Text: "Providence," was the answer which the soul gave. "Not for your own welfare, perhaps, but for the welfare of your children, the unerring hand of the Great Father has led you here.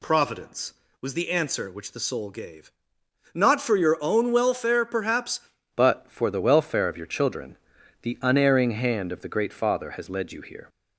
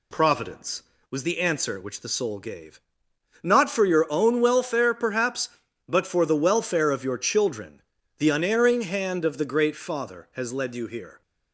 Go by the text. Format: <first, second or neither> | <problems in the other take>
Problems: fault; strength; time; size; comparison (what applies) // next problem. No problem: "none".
second | changes voice at "but"; from 5.7 s on; 4.9 s long